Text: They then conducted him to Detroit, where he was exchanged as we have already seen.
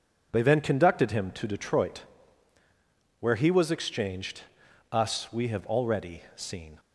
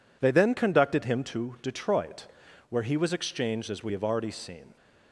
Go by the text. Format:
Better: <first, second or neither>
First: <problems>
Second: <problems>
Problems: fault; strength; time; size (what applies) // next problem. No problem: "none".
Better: second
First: says "us" for "as"; at 4.9 s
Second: none